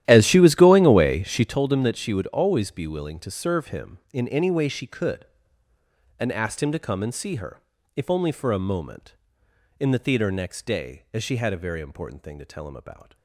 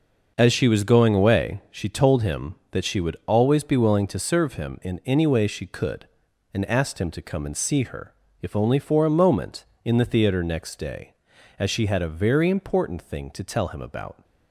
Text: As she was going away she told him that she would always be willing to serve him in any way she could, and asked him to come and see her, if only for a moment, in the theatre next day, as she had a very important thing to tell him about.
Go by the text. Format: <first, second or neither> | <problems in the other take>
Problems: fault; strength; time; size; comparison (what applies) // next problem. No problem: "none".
second | starts louder than the rest; strong; until 1.6 s; 12.5 dB